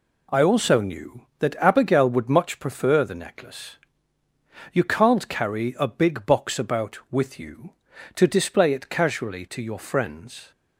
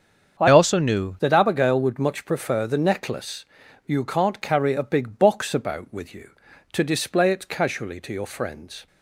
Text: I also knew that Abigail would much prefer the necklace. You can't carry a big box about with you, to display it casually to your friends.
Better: first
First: none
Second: starts louder than the rest; strong; until 1.4 s; 7 dB // changes voice from "also" to "knew"; from 0.4 to 1.1 s; 0.7 s long

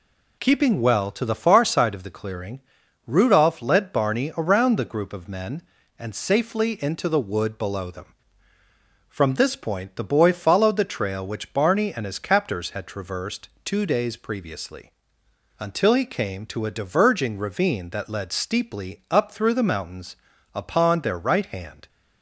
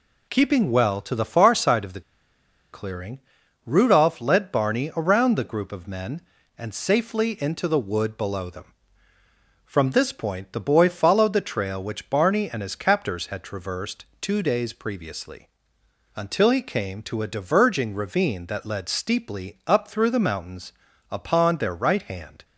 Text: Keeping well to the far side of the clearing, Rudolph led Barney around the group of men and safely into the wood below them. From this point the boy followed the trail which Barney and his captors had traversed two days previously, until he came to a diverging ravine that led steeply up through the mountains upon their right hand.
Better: first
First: pauses between "traversed" and "two"; slight; at 13.4 s; 0.16 s long // pauses between "mountains" and "upon"; at 20.1 s; 0.38 s long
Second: pauses between "the" and "clearing"; noticeable; at 2.0 s; 0.71 s long // pauses between "traversed" and "two"; slight; at 14.0 s; 0.16 s long // pauses between "mountains" and "upon"; at 20.7 s; 0.38 s long

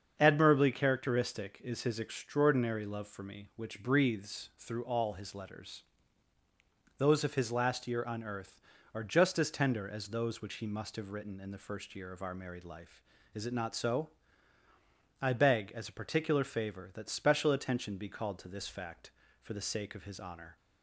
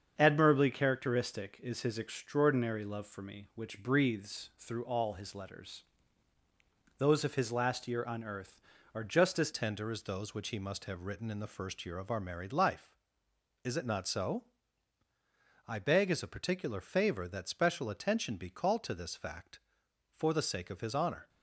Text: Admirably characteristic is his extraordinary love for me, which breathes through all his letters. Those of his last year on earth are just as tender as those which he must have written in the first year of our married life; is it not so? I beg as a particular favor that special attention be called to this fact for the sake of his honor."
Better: first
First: starts louder than the rest; strong; until 1.2 s; 7 dB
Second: starts louder than the rest; strong; until 1.1 s; 7.5 dB // changes voice at "tender"; from 9.5 s on; 11.7 s long

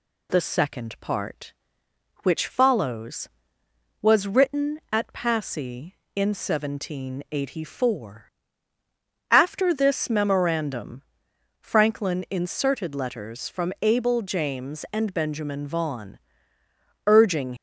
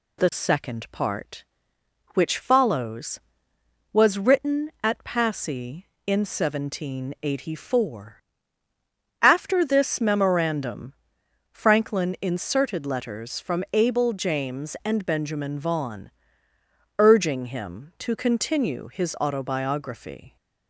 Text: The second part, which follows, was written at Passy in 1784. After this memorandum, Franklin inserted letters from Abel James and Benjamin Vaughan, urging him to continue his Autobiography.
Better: second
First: stops before "him to continue his Autobiography"; at 17.5 s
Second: none

